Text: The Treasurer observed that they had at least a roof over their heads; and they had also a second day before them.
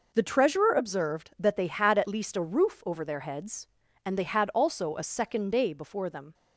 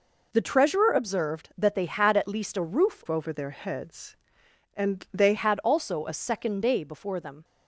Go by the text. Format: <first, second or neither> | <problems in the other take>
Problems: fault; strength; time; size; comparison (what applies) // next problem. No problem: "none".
first | changes voice from "over" to "they"; from 3.0 to 5.3 s; 2.3 s long